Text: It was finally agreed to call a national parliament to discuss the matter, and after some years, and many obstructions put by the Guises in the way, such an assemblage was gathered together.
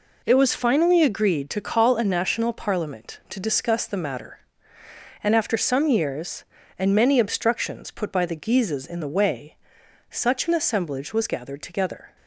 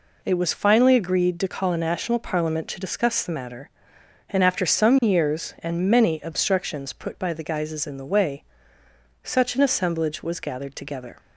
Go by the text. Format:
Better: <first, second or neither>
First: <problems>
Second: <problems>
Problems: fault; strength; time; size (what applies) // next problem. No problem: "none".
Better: second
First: gets quieter; strong; throughout; 9 dB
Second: none